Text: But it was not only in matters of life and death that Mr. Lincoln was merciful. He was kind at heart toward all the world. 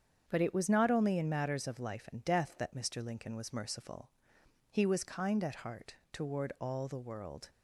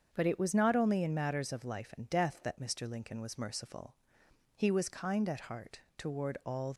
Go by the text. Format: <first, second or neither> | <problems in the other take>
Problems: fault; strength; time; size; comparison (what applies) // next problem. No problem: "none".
first | starts louder than the rest; until 1.1 s; 7 dB; strong in the first // pauses between "heart" and "toward"; slight; at 5.7 s; 0.16 s long; slight in the first // stops before "the world"; at 6.7 s